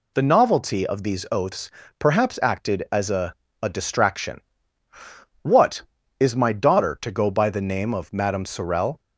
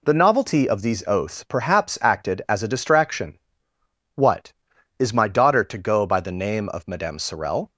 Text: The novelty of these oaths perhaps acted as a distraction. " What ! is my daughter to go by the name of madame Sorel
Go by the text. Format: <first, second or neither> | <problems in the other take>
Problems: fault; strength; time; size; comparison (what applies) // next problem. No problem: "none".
second | pauses between "oaths" and "perhaps"; slight; at 1.6 s; 0.30 s long // says "a" twice; at 3.6 s